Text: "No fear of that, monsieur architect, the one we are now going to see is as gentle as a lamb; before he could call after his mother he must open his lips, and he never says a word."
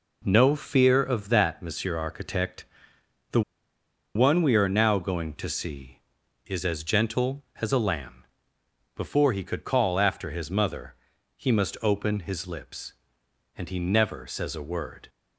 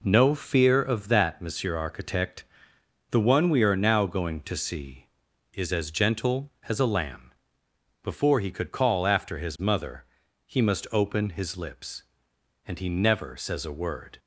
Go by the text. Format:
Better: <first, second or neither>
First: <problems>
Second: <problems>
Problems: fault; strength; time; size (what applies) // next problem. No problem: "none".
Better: second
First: pauses between "the" and "one"; noticeable; at 3.4 s; 0.74 s long // pauses between "mother" and "he"; at 10.9 s; 0.40 s long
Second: pauses between "mother" and "he"; at 10.0 s; 0.40 s long